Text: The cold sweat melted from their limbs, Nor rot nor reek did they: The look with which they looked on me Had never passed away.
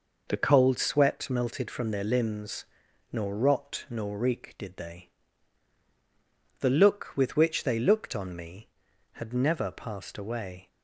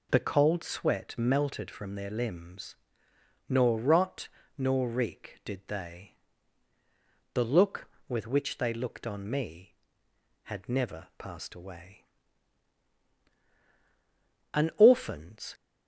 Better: first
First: none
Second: pauses between "rot" and "nor"; slight; at 4.2 s; 0.30 s long // goes on to say "An orphan's"; noticeable; from 14.5 s on; 1.0 s long

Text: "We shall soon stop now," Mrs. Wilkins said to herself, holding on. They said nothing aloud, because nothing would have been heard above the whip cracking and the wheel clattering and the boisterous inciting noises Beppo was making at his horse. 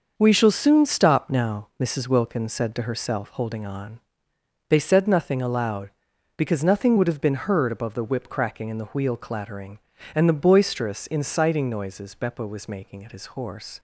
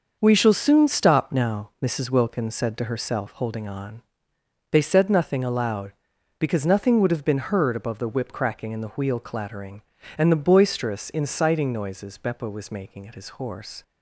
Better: neither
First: starts louder than the rest; until 1.1 s; 6.5 dB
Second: starts louder than the rest; until 1.2 s; 6.5 dB

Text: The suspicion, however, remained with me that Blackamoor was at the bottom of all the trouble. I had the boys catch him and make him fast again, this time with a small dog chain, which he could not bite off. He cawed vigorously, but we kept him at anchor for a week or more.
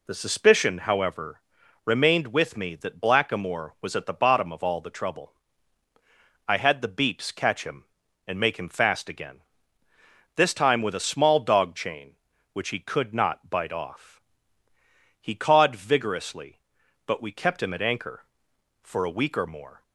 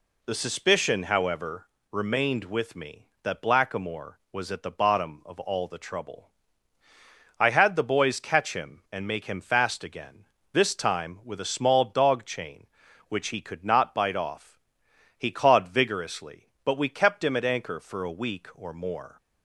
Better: second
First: says "beeps" for "boys"; at 6.8 s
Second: none

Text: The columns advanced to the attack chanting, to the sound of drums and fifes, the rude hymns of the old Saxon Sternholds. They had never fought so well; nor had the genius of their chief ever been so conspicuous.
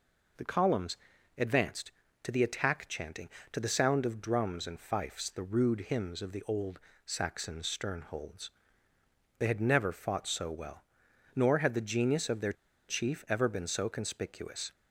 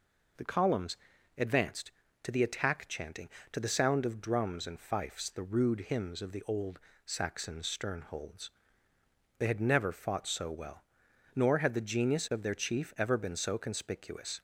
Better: second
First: pauses between "columns" and "advanced"; at 0.9 s; 0.42 s long // pauses between "old" and "Saxon"; slight; at 6.7 s; 0.26 s long // pauses between "their" and "chief"; at 12.5 s; 0.36 s long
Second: pauses between "columns" and "advanced"; at 0.9 s; 0.42 s long // pauses between "old" and "Saxon"; slight; at 6.7 s; 0.26 s long

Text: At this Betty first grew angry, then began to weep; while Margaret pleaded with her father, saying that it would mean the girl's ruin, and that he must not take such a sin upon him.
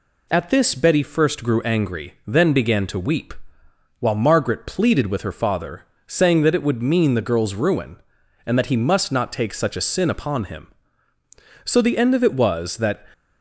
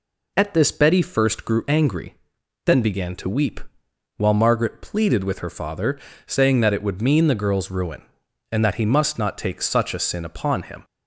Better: second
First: goes on to say "So the end of it was that"; from 11.6 s on; 1.4 s long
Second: none

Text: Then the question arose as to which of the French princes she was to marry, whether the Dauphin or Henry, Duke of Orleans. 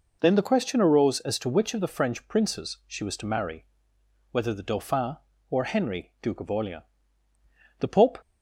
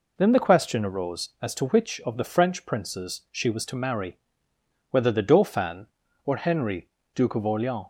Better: second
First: goes on to say "The Pope"; slight; from 7.7 s on; 0.40 s long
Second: none

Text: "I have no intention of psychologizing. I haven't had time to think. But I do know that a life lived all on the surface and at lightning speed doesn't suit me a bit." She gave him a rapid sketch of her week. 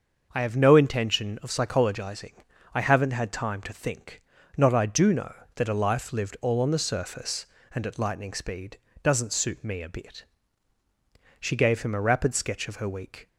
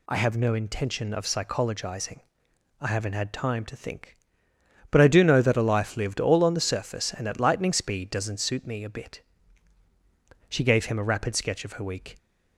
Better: second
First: starts louder than the rest; until 1.3 s; 6.5 dB // says "Not" for "But"; at 4.5 s // pauses between "speed" and "doesn't"; slight; at 8.7 s; 0.24 s long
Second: none

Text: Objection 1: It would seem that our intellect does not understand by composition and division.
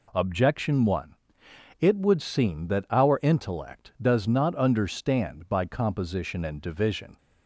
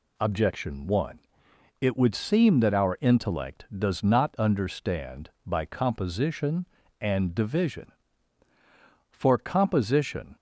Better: first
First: none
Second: goes on to say "For composition"; noticeable; from 9.0 s on; 1.2 s long

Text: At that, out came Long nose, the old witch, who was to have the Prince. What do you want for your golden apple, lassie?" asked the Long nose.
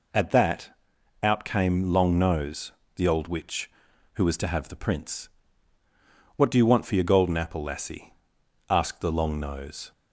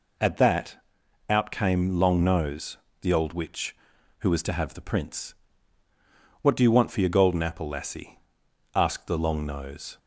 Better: neither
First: none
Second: none

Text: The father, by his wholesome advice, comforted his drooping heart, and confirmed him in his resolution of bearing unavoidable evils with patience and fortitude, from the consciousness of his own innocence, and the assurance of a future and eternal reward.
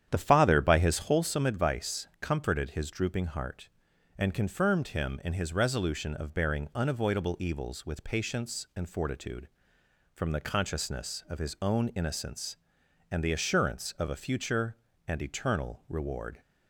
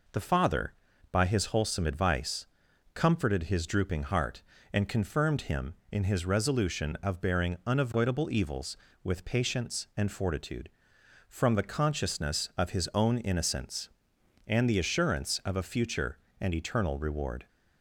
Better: second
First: starts louder than the rest; strong; until 1.2 s; 9.5 dB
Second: none

